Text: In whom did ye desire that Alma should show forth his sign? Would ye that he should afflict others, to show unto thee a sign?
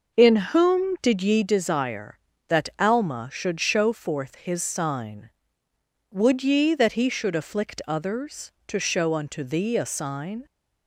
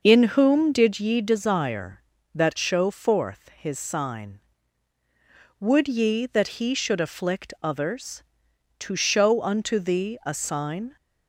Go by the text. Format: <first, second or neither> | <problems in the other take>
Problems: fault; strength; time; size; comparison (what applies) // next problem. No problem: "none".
first | skips "Alma should"; at 2.5 s